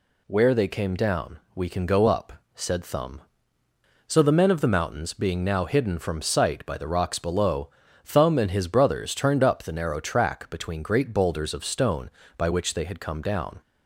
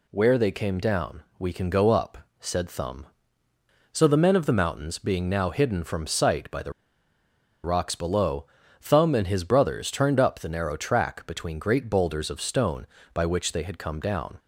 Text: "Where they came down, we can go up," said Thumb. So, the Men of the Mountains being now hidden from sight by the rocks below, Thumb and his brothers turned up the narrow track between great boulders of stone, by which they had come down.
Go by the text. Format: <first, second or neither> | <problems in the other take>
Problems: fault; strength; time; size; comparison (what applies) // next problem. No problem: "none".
first | pauses between "the" and "rocks"; noticeable; at 6.7 s; 0.92 s long